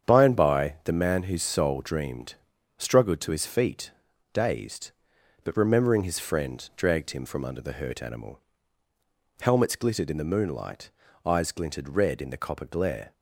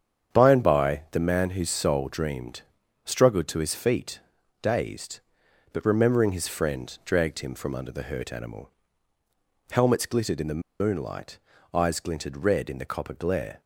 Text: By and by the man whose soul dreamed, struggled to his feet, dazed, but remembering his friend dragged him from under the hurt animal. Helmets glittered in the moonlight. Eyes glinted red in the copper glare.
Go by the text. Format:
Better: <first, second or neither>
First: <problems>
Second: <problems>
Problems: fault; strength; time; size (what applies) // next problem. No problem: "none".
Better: first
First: starts louder than the rest; strong; until 1.1 s; 8 dB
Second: starts louder than the rest; strong; until 1.4 s; 8 dB // pauses between "the" and "moonlight"; slight; at 10.6 s; 0.18 s long